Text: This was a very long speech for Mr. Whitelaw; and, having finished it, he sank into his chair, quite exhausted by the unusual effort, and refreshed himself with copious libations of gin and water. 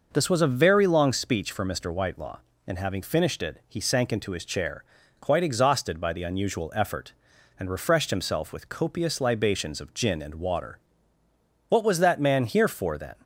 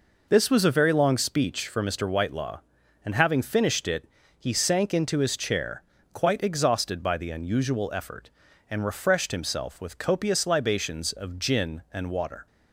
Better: second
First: goes on to say "What was that man here for then"; from 11.6 s on; 1.4 s long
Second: none

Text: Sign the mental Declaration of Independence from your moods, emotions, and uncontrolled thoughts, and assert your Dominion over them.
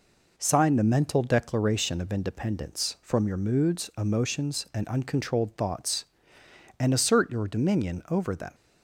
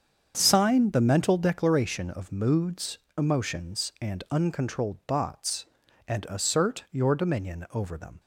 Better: first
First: none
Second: starts louder than the rest; strong; until 1.3 s; 7.5 dB // skips "Independence from your"; at 2.2 s

